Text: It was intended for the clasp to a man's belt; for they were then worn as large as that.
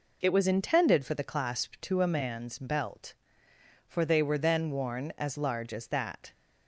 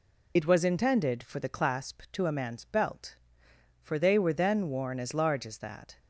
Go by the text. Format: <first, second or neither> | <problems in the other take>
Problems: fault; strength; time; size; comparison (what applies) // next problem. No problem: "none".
first | loses the start of "It"; at 0.3 s; 55 ms